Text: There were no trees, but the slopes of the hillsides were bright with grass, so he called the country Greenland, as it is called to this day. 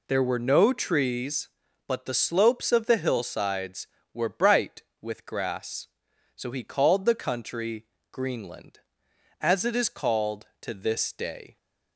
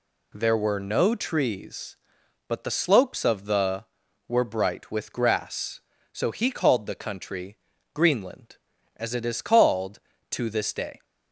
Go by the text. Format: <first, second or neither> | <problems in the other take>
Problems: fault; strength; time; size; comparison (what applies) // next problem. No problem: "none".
first | skips "hillsides"; at 4.0 s // pauses between "country" and "Greenland"; slight; at 7.5 s; 0.36 s long; slight in the first